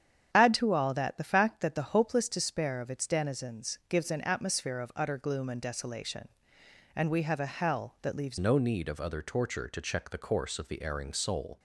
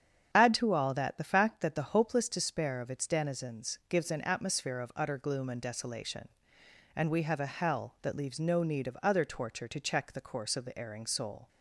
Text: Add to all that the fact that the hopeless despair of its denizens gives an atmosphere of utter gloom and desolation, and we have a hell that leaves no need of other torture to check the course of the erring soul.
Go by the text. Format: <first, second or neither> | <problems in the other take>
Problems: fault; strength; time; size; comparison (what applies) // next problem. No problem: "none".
second | starts louder than the rest; strong; until 1.3 s; 8.5 dB; strong in the second // changes voice at "no"; from 8.3 s on; 3.2 s long